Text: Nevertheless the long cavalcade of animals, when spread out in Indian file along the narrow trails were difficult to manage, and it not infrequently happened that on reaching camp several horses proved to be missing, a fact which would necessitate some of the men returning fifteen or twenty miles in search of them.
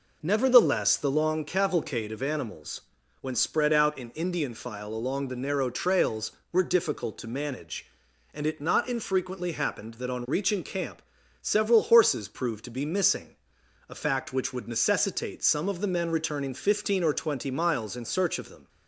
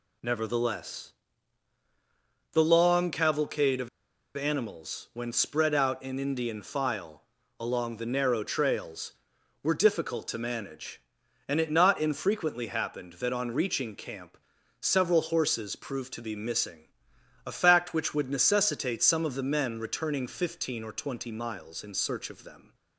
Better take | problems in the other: first | pauses between "Nevertheless" and "the"; strong; at 1.1 s; 1.4 s long // pauses between "of" and "animals"; noticeable; at 3.8 s; 0.47 s long // pauses between "file" and "along"; at 7.2 s; 0.38 s long // pauses between "camp" and "several"; at 14.3 s; 0.42 s long; also in the first

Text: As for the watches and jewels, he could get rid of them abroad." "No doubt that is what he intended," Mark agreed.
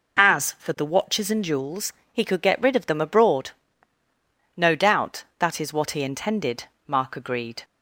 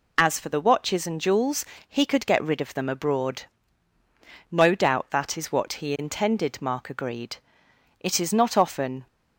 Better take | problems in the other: first | goes on to say "It is not often"; noticeable; from 8.0 s on; 1.0 s long

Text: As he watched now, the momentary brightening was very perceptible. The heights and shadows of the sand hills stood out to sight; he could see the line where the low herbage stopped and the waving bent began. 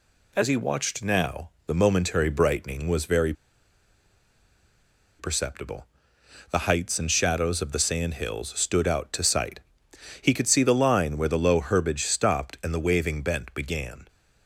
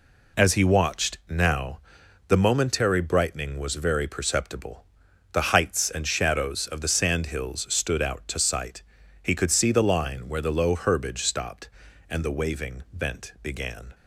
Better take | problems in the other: second | pauses between "very" and "perceptible"; strong; at 3.3 s; 1.8 s long

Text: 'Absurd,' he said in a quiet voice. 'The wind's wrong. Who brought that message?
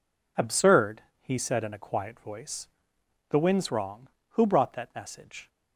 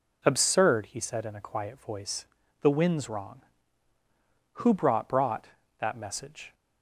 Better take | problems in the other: first | says "brought" twice; at 5.0 s

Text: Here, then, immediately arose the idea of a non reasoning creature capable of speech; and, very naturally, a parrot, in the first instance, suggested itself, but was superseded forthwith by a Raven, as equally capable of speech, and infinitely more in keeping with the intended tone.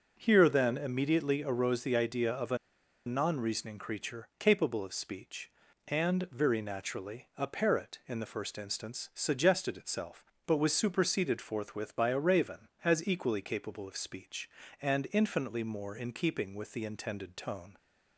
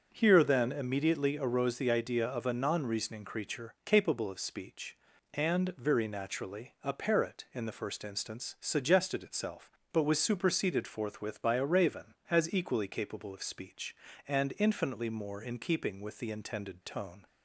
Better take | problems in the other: second | starts louder than the rest; until 1.1 s; 6.5 dB; also in the second // pauses between "a" and "non"; noticeable; at 2.5 s; 0.49 s long

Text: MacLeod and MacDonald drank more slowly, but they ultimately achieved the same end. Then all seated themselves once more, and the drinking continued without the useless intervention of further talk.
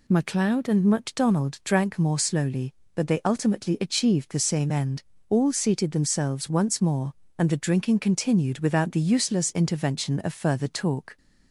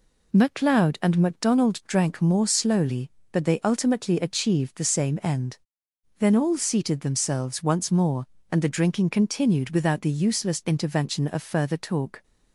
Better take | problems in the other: second | skips "Then"; at 5.1 s

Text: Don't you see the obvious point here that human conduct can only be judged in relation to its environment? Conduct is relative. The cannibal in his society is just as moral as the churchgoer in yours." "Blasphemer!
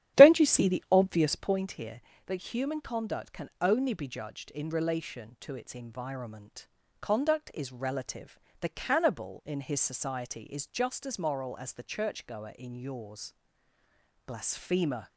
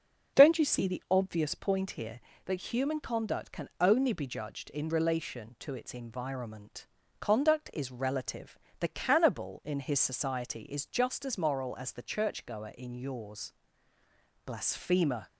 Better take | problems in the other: second | starts louder than the rest; strong; until 1.6 s; 11.5 dB

